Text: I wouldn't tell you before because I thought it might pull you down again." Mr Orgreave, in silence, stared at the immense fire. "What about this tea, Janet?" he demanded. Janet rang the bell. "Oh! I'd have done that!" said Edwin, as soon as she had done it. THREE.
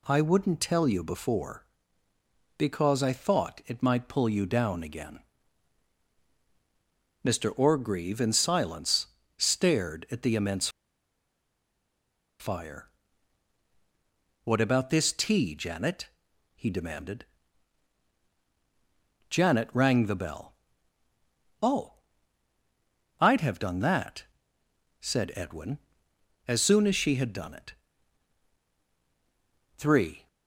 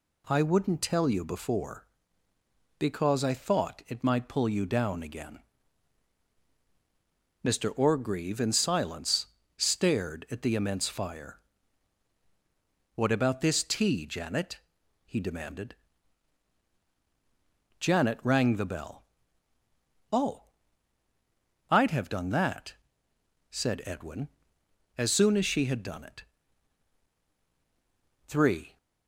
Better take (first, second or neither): second